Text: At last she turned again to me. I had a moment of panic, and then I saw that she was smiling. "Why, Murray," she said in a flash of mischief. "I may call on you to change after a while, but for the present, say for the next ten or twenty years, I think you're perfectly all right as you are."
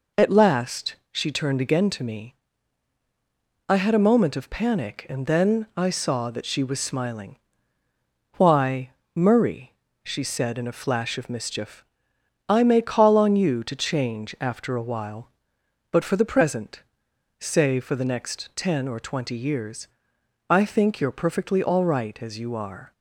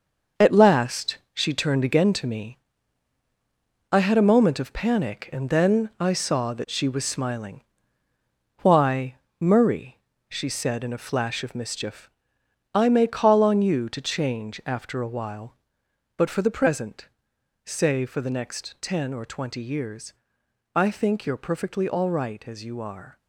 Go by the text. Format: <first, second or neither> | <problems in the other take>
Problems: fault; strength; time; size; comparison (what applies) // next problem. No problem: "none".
first | gets quieter; strong; throughout; 9 dB // pauses between "last" and "she"; slight; at 1.1 s; 0.18 s long; slight in the first